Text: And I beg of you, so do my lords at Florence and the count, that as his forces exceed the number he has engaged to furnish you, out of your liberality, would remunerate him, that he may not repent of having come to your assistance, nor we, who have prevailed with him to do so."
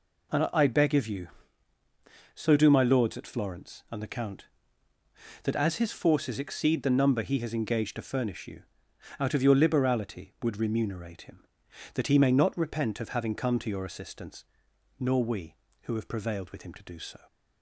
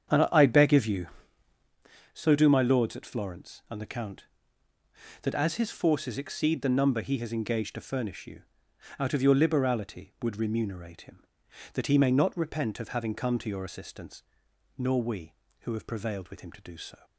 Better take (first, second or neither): first